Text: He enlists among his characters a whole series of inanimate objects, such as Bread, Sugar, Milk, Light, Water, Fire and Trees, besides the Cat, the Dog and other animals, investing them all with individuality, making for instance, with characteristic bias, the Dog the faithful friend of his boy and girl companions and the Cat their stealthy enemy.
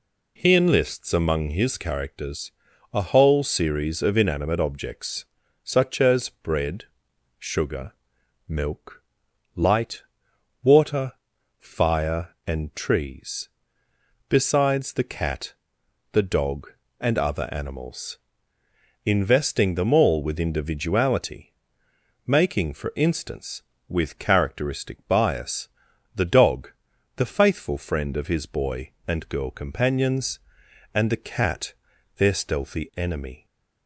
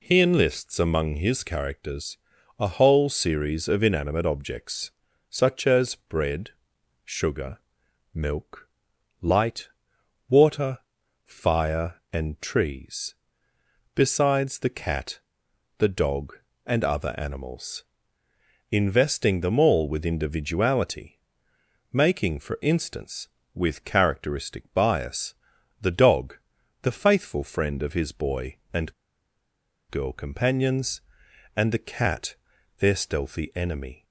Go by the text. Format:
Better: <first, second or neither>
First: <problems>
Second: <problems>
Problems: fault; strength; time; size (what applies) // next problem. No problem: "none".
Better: first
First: pauses between "characters" and "a"; at 2.5 s; 0.40 s long // pauses between "Dog" and "the"; noticeable; at 26.7 s; 0.46 s long // pauses between "Cat" and "their"; noticeable; at 31.7 s; 0.46 s long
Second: pauses between "characters" and "a"; at 2.1 s; 0.40 s long // pauses between "Dog" and "the"; noticeable; at 26.3 s; 0.46 s long // pauses between "and" and "girl"; noticeable; at 28.9 s; 0.97 s long // pauses between "Cat" and "their"; noticeable; at 32.3 s; 0.46 s long